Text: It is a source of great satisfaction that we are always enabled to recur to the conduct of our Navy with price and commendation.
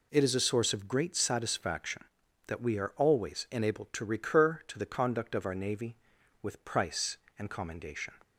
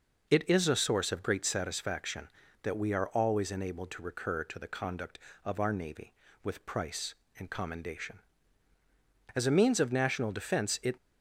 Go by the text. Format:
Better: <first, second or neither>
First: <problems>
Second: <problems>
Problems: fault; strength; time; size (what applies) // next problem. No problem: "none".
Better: first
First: none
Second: goes on to say "As a means of national defense it"; from 9.3 s on; 1.6 s long